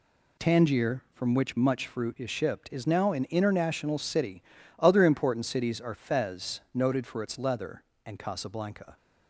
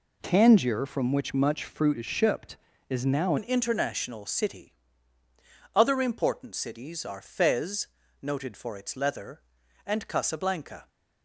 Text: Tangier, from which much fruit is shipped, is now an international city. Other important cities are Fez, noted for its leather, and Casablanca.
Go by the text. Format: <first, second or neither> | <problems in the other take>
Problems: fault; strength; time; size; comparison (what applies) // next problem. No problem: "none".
first | changes voice at "an"; from 3.3 s on; 7.5 s long